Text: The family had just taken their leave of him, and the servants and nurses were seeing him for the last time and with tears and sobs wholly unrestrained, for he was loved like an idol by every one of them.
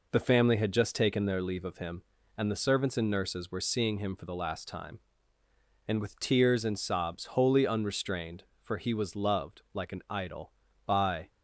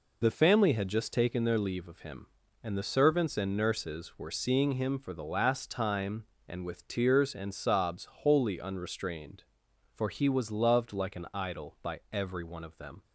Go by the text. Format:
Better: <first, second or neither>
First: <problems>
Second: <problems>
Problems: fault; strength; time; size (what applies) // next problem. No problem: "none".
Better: second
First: stops before "every one of them"; at 11.2 s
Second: none